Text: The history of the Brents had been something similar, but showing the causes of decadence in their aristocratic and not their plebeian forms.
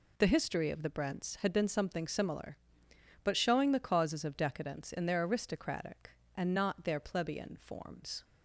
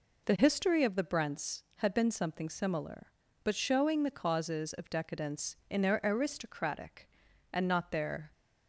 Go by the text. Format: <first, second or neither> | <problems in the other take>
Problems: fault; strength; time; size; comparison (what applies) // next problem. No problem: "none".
first | stops before "plebeian forms"; at 8.3 s